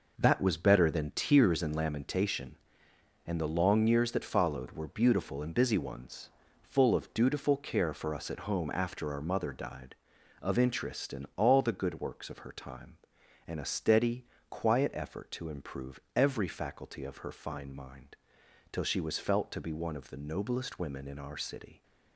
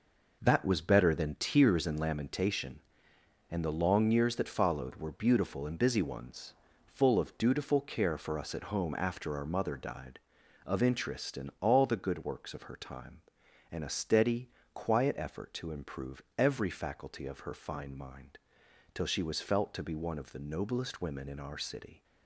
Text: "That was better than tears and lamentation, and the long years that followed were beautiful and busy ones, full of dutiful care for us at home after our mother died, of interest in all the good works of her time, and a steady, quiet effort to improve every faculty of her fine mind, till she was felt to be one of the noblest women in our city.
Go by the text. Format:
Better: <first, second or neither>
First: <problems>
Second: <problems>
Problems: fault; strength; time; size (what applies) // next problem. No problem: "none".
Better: neither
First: pauses between "improve" and "every"; slight; at 15.9 s; 0.16 s long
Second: pauses between "improve" and "every"; slight; at 16.2 s; 0.16 s long